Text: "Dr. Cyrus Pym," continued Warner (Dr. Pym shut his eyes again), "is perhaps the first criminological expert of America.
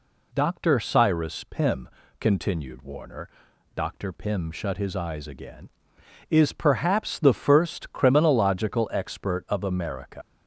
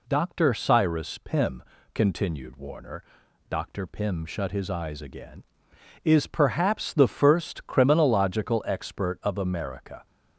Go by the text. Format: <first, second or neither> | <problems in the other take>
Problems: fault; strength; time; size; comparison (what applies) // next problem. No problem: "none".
second | leaves "America" unfinished; at 10.2 s; 95 ms